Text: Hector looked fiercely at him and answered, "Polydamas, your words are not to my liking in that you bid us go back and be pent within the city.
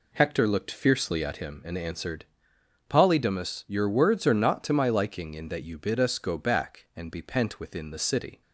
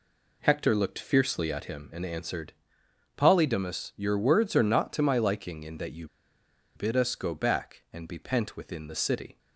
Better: first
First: none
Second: pauses between "you" and "bid"; noticeable; at 6.0 s; 0.68 s long

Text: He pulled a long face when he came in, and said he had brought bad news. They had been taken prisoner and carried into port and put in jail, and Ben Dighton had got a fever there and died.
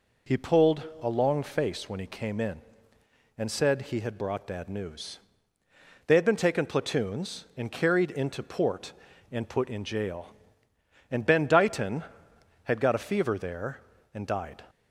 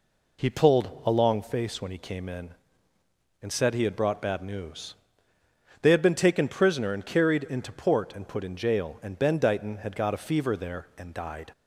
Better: second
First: pauses between "pulled" and "a"; slight; at 0.8 s; 0.18 s long // says "platoons" for "prisoner"; at 6.6 s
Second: none

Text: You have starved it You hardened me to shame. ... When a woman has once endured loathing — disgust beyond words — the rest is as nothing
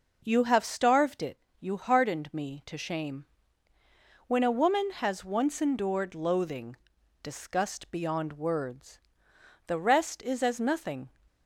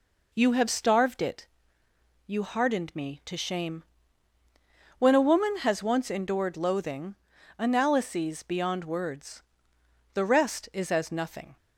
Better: first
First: pauses between "it" and "You"; slight; at 1.3 s; 0.22 s long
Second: pauses between "it" and "You"; noticeable; at 1.4 s; 0.80 s long // says "analyses" for "disgust"; at 7.5 s

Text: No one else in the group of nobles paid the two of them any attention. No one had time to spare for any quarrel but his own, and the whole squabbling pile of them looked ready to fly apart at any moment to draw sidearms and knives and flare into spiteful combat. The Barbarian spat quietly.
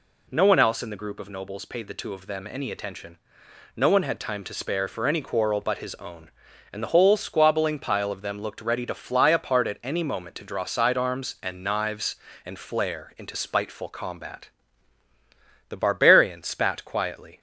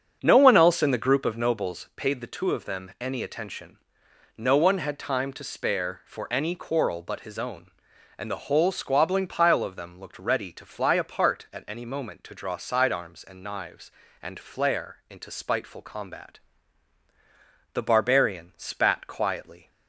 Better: first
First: none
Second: starts louder than the rest; until 2.0 s; 7 dB

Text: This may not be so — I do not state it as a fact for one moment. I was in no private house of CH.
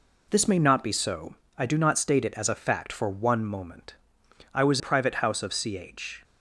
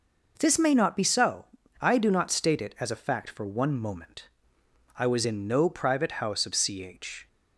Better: second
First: skips "in no"; at 4.7 s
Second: none

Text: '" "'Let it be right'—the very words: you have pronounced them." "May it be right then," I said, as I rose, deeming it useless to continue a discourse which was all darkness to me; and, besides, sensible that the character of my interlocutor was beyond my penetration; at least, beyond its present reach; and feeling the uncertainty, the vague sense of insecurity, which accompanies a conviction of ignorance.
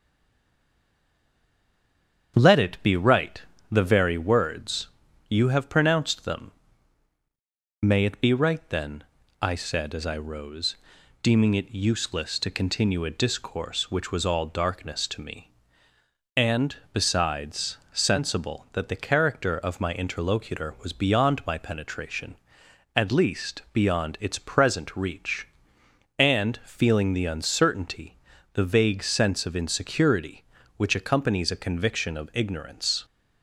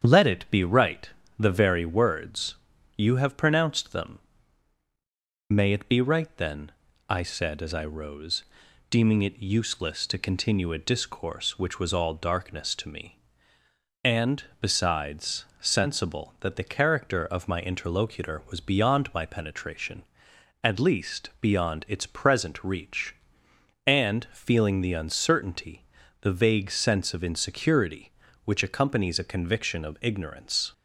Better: second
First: stays silent before the first word; until 2.3 s; 2.3 s long // starts louder than the rest; strong; until 3.3 s; 8 dB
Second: starts louder than the rest; strong; until 1.0 s; 8 dB

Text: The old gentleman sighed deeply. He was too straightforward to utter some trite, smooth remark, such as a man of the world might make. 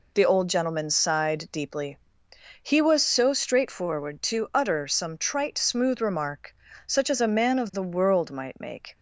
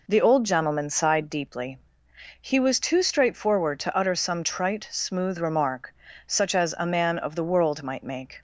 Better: second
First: says "so" for "too"; at 3.0 s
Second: none

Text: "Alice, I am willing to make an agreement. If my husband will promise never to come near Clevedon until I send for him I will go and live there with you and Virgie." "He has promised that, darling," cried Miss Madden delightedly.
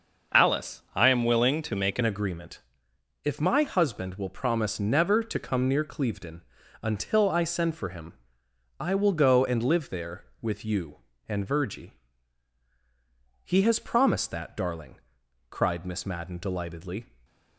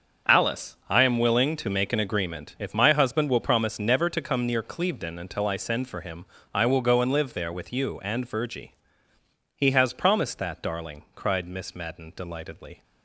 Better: second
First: starts louder than the rest; until 1.4 s; 6 dB // changes voice at "agreement"; from 2.0 s on; 15.0 s long // pauses between "Clevedon" and "until"; at 6.4 s; 0.40 s long // pauses between "him" and "I"; noticeable; at 8.1 s; 0.66 s long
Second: starts louder than the rest; until 1.3 s; 6.5 dB // pauses between "him" and "I"; slight; at 6.2 s; 0.28 s long

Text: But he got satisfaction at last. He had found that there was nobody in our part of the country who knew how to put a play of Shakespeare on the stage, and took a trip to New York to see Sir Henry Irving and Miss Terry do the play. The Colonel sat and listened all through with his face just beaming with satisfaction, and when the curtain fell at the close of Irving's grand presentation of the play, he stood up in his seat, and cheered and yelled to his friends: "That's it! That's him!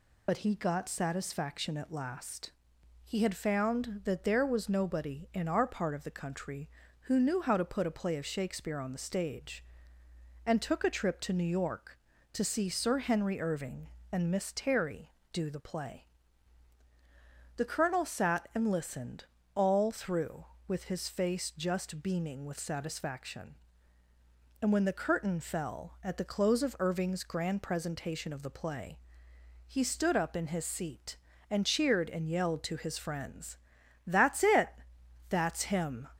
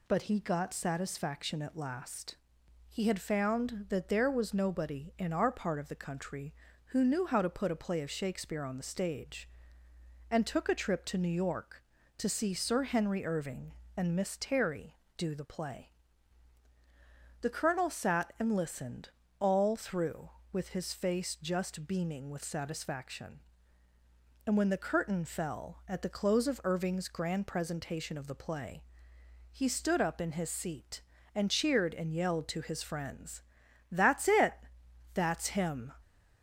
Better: second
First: loses the start of "But"; at 0.2 s; 55 ms // pauses between "listened" and "all"; slight; at 19.2 s; 0.30 s long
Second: pauses between "listened" and "all"; slight; at 19.0 s; 0.30 s long

